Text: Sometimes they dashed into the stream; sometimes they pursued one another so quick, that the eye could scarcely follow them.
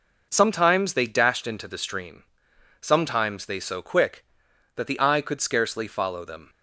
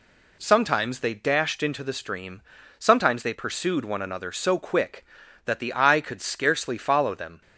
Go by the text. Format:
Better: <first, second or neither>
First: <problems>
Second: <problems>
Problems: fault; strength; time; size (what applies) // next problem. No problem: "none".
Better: second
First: skips "pursued one another"; at 3.5 s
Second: none